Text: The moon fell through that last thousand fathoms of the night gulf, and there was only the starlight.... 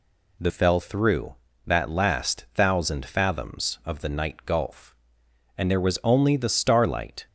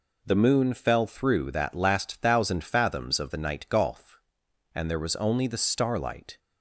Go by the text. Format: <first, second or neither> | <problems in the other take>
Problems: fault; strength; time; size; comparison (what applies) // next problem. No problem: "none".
second | skips "moon"; at 0.4 s